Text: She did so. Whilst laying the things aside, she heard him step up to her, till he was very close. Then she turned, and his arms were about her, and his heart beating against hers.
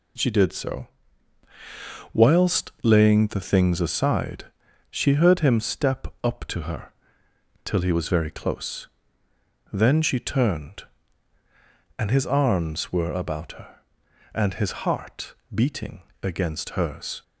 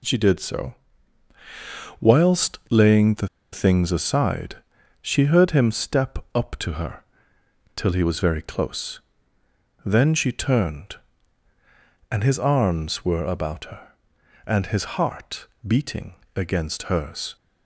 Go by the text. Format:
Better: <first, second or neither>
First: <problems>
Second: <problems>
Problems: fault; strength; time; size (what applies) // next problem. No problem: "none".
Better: first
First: pauses between "step" and "up"; slight; at 6.0 s; 0.18 s long // pauses between "heart" and "beating"; slight; at 15.3 s; 0.18 s long // pauses between "beating" and "against"; slight; at 16.0 s; 0.21 s long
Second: pauses between "the" and "things"; slight; at 3.2 s; 0.24 s long // pauses between "step" and "up"; slight; at 6.1 s; 0.18 s long // pauses between "heart" and "beating"; slight; at 15.4 s; 0.18 s long // pauses between "beating" and "against"; slight; at 16.1 s; 0.22 s long